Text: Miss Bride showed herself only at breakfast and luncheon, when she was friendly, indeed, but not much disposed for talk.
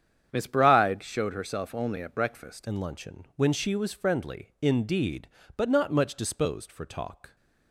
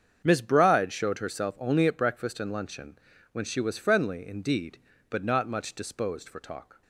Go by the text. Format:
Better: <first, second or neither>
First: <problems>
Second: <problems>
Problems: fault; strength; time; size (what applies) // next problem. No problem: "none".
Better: second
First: starts louder than the rest; strong; until 1.3 s; 8 dB // changes voice at "and"; from 2.6 s on; 4.7 s long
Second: starts louder than the rest; strong; until 1.2 s; 7.5 dB